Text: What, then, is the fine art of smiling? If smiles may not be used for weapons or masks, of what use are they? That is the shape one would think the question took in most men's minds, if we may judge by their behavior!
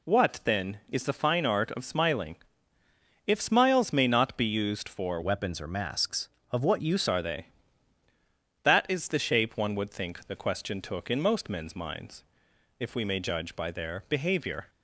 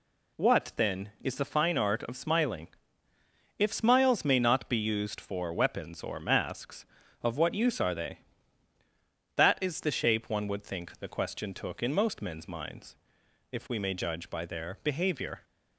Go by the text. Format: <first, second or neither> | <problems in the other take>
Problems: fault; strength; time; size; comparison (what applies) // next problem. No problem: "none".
second | changes voice from "weapons" to "use"; from 5.2 to 7.0 s; 1.8 s long